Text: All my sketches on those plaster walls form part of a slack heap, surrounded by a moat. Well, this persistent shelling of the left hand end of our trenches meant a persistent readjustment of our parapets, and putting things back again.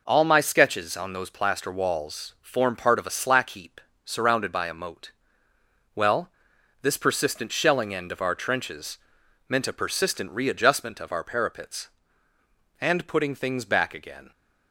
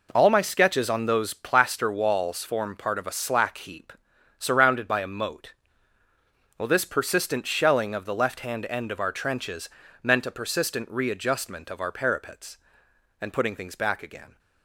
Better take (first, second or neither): second